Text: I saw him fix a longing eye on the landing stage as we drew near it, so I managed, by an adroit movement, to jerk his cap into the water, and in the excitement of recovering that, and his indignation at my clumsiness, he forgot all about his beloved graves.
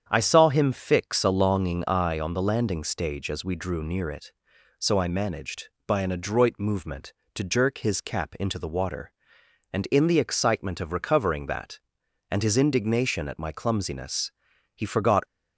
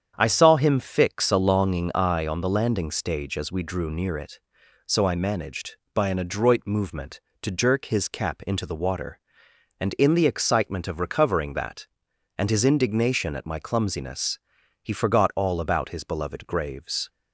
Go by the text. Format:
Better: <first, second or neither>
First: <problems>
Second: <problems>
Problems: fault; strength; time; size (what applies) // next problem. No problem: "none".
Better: second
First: starts louder than the rest; strong; until 1.0 s; 8 dB // stops before "all about his beloved graves"; at 15.2 s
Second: starts louder than the rest; strong; until 1.1 s; 8 dB